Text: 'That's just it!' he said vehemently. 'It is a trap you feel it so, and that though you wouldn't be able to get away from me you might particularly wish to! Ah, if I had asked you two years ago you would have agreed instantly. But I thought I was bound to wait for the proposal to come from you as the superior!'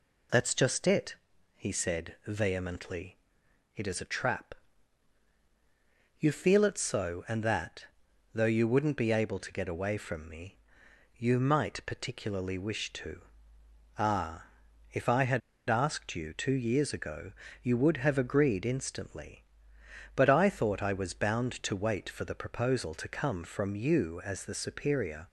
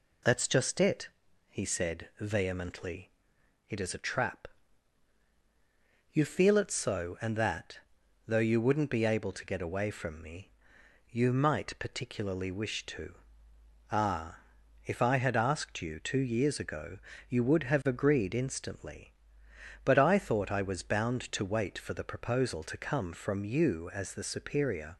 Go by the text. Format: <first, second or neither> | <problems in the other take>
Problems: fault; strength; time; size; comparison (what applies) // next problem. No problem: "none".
second | pauses between "trap" and "you"; strong; at 4.5 s; 1.6 s long; strong in the second // pauses between "that" and "though"; noticeable; at 7.8 s; 0.48 s long; noticeable in the second // pauses between "me" and "you"; noticeable; at 10.5 s; 0.62 s long; noticeable in the second // pauses between "had" and "asked"; slight; at 15.4 s; 0.29 s long // pauses between "ago" and "you"; slight; at 17.3 s; 0.28 s long; slight in the second